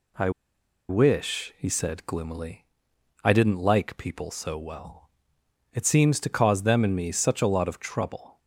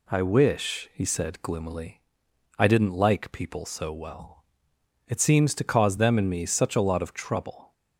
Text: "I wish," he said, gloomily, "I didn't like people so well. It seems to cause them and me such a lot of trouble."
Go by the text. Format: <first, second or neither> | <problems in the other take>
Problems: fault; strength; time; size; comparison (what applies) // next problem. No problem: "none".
second | pauses between "I" and "wish"; noticeable; at 0.2 s; 0.59 s long